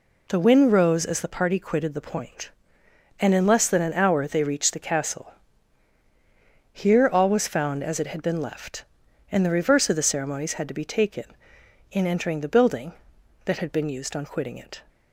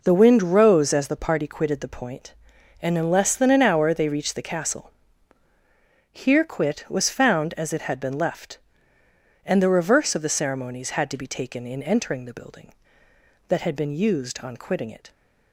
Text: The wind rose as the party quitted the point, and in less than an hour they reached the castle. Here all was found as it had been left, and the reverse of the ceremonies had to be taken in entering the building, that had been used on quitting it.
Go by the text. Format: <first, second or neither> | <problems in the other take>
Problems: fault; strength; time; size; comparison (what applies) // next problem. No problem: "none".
first | says "quit" for "all"; at 6.4 s